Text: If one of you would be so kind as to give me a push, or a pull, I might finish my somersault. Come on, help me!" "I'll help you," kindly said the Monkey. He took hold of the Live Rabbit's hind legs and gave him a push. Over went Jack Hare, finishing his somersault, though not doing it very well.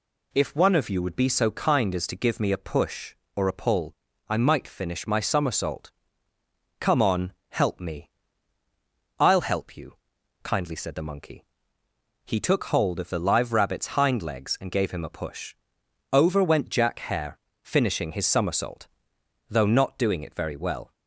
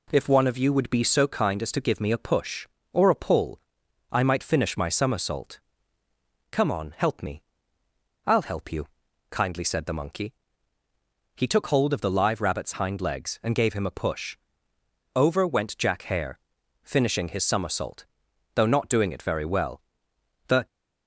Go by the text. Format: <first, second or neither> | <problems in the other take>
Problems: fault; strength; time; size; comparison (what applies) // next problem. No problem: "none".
first | goes on to say "The"; slight; from 20.4 s on; 0.18 s long